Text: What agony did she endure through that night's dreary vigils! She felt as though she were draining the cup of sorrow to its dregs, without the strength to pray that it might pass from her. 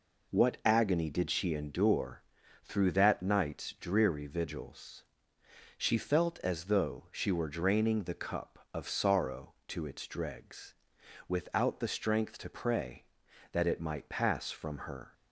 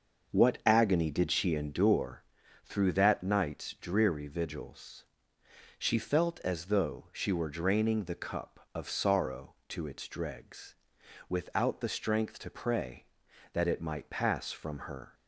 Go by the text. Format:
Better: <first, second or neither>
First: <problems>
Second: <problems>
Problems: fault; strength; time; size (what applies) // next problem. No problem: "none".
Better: first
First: pauses between "endure" and "through"; at 2.2 s; 0.44 s long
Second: starts louder than the rest; until 2.1 s; 6 dB // pauses between "endure" and "through"; at 2.2 s; 0.44 s long